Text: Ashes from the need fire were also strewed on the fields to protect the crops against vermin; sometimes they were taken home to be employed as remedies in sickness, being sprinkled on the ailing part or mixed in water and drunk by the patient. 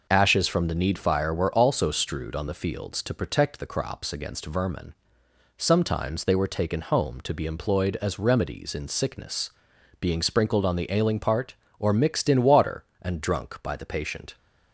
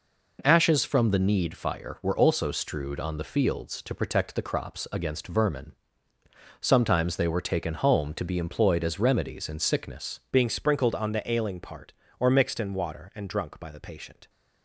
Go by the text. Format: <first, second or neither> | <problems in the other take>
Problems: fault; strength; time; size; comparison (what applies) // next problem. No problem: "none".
first | changes voice at "being"; from 10.3 s on; 3.9 s long